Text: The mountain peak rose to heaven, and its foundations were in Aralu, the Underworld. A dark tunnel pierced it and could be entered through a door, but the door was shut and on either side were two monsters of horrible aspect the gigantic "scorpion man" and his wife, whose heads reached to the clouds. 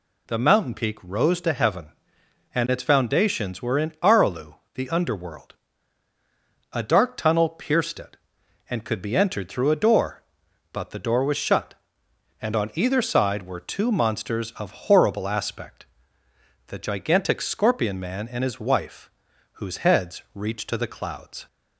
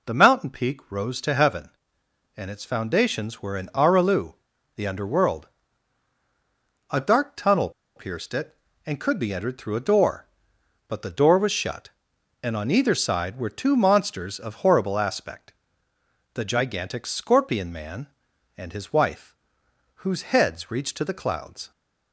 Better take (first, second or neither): first